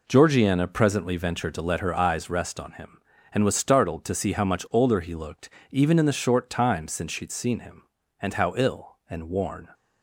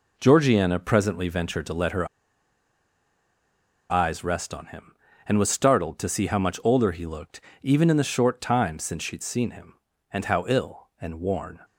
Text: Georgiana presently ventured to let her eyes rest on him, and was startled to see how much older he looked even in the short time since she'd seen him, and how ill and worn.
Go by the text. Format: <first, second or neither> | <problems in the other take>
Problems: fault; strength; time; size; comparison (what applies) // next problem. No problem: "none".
first | pauses between "her" and "eyes"; strong; at 2.0 s; 1.8 s long // pauses between "looked" and "even"; slight; at 7.4 s; 0.20 s long; slight in the first